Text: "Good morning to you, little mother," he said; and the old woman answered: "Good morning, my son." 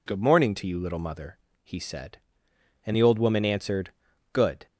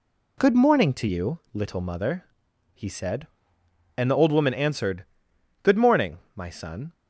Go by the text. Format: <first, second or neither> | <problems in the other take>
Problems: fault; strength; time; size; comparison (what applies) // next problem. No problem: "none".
second | stops before "morning my son"; at 4.6 s